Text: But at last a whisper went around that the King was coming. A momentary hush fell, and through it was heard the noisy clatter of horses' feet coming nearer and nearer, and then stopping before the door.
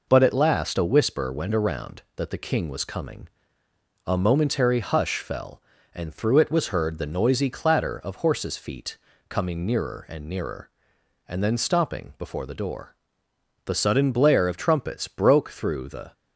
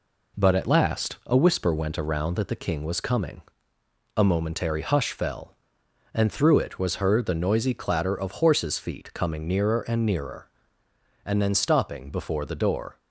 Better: second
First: pauses between "feet" and "coming"; slight; at 8.9 s; 0.32 s long // goes on to say "The sudden blare of trumpets broke through the"; strong; from 13.6 s on; 2.4 s long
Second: none

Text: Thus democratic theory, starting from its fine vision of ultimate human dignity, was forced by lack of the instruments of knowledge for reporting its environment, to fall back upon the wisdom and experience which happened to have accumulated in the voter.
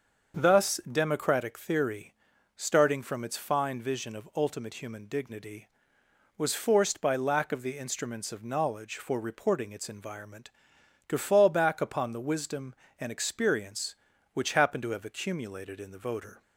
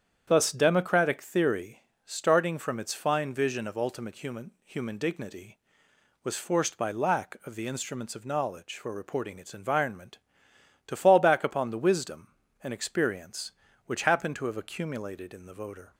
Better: first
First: starts louder than the rest; until 1.3 s; 6.5 dB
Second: starts louder than the rest; strong; until 1.2 s; 8.5 dB // says "human" twice; at 4.6 s

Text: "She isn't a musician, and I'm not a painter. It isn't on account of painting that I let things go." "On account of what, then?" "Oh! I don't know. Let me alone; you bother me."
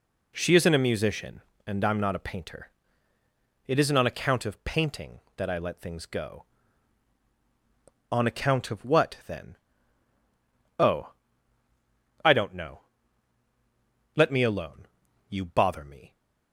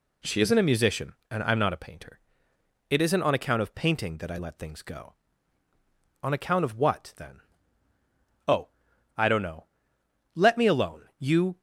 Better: first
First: none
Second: stops before "bother me"; at 11.5 s

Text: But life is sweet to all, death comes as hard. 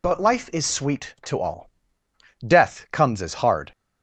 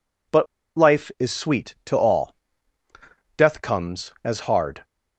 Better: first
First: none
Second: pauses between "But" and "life"; slight; at 0.4 s; 0.30 s long

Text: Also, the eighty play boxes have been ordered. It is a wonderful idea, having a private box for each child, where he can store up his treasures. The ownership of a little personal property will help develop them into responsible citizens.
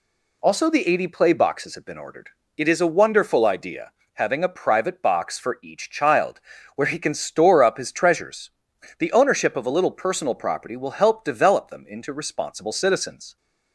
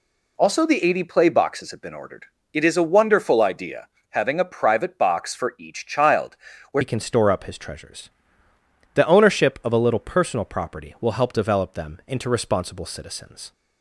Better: first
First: none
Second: changes voice at "he"; from 6.8 s on; 6.7 s long

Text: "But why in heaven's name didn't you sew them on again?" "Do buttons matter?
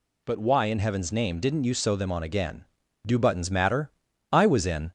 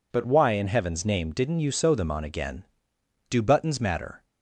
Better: second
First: goes on to say "I was in"; from 4.3 s on; 0.60 s long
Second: none

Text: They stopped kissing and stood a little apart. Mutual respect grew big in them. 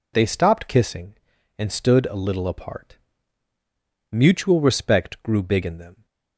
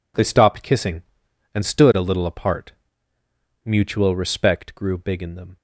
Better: neither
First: none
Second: none

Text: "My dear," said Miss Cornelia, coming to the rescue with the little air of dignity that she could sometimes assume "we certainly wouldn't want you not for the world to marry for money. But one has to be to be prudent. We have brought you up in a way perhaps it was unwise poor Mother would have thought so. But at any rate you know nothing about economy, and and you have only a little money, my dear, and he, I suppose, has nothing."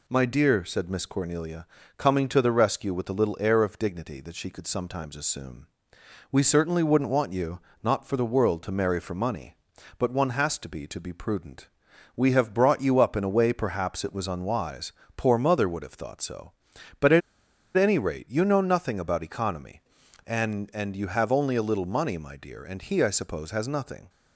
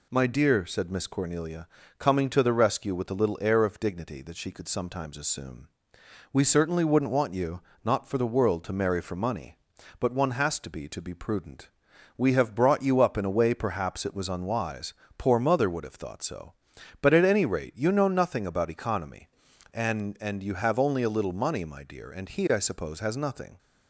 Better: second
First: pauses between "assume" and "we"; noticeable; at 5.6 s; 0.66 s long // pauses between "you" and "not"; slight; at 7.5 s; 0.24 s long // pauses between "unwise" and "poor"; slight; at 14.9 s; 0.24 s long // pauses between "at" and "any"; noticeable; at 17.2 s; 0.56 s long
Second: pauses between "assume" and "we"; noticeable; at 5.6 s; 0.66 s long // pauses between "you" and "not"; slight; at 7.5 s; 0.24 s long // pauses between "unwise" and "poor"; slight; at 14.9 s; 0.24 s long

